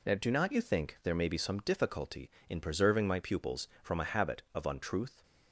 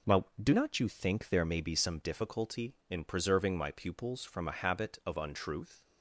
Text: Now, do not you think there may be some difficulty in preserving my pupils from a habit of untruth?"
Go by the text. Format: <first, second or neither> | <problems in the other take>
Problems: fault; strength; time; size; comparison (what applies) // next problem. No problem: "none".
neither | none